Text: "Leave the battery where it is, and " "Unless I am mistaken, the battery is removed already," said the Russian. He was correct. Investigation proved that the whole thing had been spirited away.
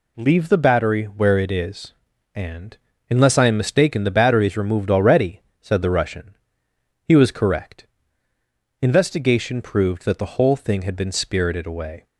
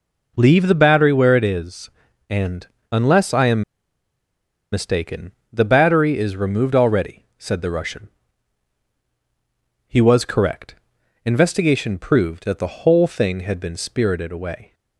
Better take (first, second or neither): first